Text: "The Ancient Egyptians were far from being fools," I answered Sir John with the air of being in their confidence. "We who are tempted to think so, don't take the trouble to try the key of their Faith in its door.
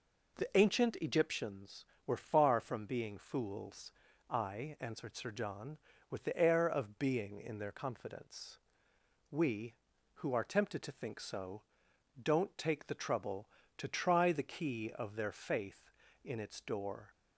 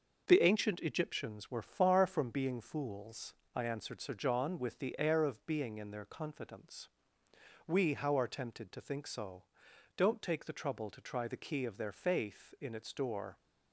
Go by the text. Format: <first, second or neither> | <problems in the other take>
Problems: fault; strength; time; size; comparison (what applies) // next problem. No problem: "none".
first | starts louder than the rest; until 1.2 s; 6 dB // says "how" for "who"; at 7.9 s